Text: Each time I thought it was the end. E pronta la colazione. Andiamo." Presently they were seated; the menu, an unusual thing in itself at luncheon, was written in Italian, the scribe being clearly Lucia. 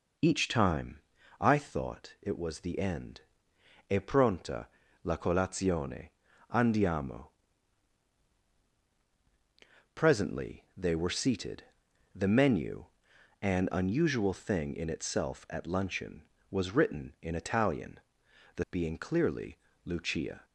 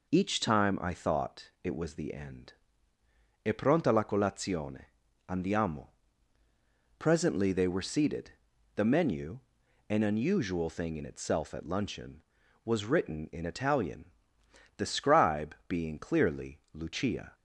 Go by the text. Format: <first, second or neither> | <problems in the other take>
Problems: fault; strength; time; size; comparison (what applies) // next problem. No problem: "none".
second | pauses between "time" and "I"; at 0.9 s; 0.42 s long // pauses between "pronta" and "la"; at 4.6 s; 0.38 s long // skips "scribe"; at 18.6 s // pauses between "clearly" and "Lucia"; slight; at 19.5 s; 0.26 s long